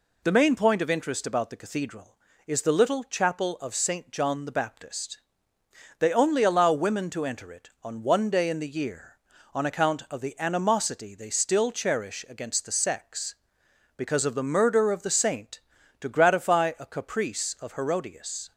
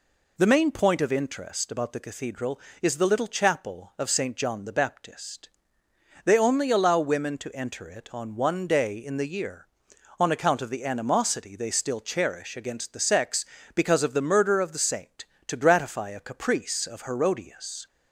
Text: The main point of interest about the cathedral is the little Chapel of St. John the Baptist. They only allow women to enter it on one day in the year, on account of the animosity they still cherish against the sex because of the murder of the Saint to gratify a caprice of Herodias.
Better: neither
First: none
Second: none

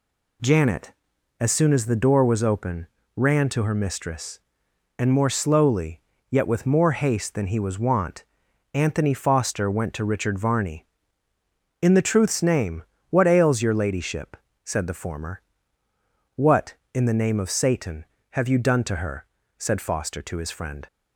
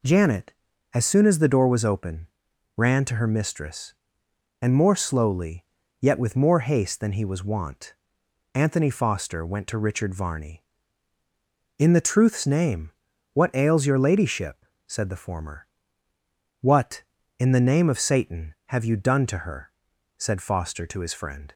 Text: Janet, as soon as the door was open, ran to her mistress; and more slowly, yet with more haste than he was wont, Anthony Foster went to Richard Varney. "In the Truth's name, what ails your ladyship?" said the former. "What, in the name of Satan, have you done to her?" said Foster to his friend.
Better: neither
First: none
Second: none

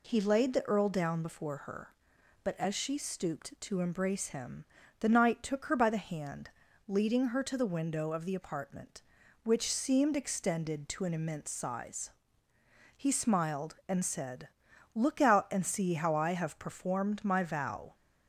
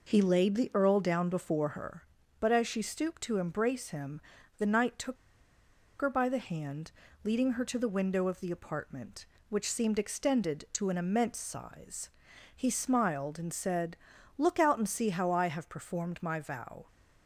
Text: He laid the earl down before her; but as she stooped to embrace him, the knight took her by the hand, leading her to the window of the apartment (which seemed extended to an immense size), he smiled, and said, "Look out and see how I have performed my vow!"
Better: first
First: none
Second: pauses between "took" and "her"; noticeable; at 5.1 s; 0.84 s long

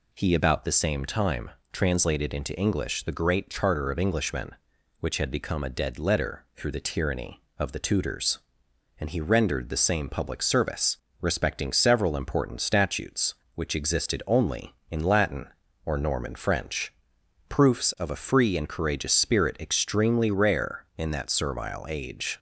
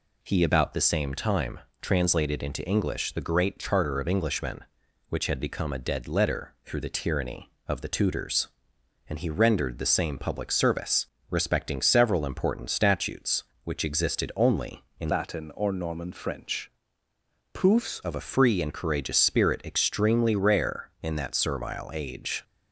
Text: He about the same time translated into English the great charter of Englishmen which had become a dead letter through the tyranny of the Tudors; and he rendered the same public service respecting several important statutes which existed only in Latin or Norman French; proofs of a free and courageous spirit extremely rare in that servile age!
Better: first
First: pauses between "time" and "translated"; slight; at 1.4 s; 0.22 s long // pauses between "service" and "respecting"; slight; at 10.9 s; 0.24 s long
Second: pauses between "time" and "translated"; slight; at 1.5 s; 0.22 s long // pauses between "service" and "respecting"; slight; at 11.0 s; 0.24 s long // changes voice from "Latin" to "proofs"; from 15.1 to 18.0 s; 2.9 s long

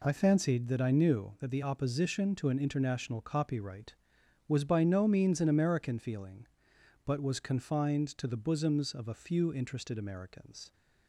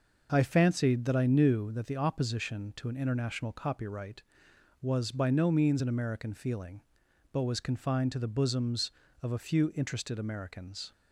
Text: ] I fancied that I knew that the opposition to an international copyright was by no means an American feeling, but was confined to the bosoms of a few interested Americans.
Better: neither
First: none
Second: none

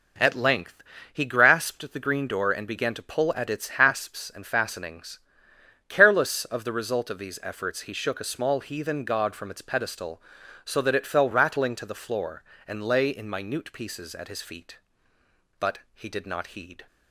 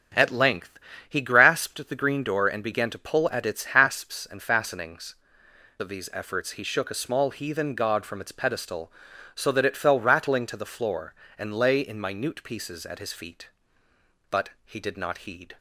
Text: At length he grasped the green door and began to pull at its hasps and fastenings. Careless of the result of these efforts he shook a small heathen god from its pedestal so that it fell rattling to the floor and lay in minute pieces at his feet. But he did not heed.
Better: first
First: pauses between "length" and "he"; slight; at 0.8 s; 0.30 s long // pauses between "But" and "he"; slight; at 15.7 s; 0.16 s long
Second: starts louder than the rest; strong; until 1.4 s; 7.5 dB // pauses between "length" and "he"; slight; at 0.7 s; 0.30 s long // skips "Careless of the result"; at 5.4 s // pauses between "But" and "he"; slight; at 14.4 s; 0.16 s long

